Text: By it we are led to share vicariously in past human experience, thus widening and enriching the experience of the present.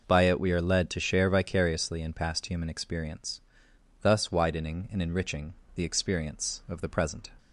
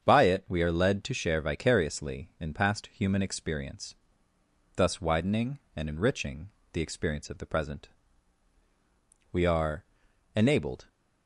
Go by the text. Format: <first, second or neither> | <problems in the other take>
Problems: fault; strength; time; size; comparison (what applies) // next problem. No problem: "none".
first | starts louder than the rest; strong; until 1.0 s; 7.5 dB // pauses between "enriching" and "the"; slight; at 6.4 s; 0.22 s long; slight in the first // goes on to say "We are enabled"; from 9.3 s on; 1.5 s long